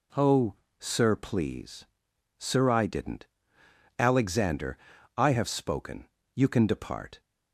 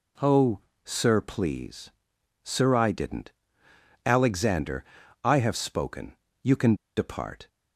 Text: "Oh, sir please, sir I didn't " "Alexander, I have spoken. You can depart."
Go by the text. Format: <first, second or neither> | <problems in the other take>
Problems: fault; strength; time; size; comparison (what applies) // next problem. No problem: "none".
first | pauses between "can" and "depart"; slight; at 6.7 s; 0.22 s long